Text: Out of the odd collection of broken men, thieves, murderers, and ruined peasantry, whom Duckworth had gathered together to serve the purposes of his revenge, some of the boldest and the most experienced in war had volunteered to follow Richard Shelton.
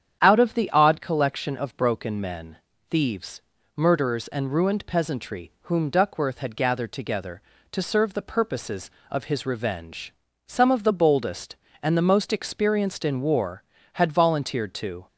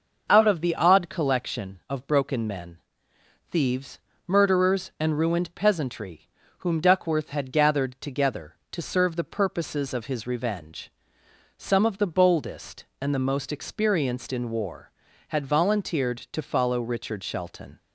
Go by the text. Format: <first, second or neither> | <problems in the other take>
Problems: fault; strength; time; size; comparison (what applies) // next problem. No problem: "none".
second | starts louder than the rest; strong; until 1.2 s; 9 dB; noticeable in the second // stops before "follow Richard Shelton"; at 15.0 s